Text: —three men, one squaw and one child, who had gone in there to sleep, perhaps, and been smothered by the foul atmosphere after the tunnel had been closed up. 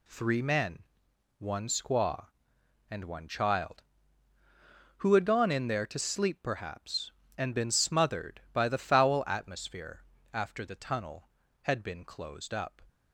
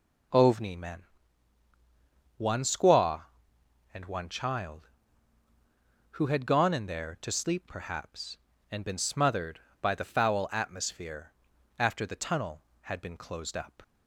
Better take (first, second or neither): first